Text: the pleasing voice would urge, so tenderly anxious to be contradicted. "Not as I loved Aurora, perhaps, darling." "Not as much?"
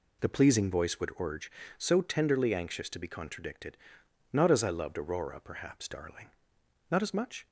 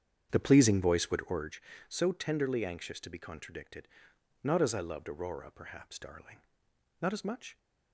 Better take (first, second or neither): first